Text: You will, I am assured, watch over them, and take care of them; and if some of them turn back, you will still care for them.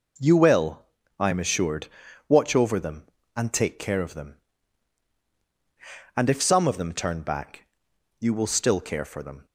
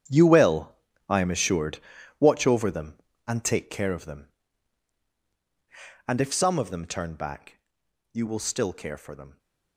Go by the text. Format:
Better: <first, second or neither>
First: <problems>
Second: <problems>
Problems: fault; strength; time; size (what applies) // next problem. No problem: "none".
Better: first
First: none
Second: gets quieter; strong; throughout; 15 dB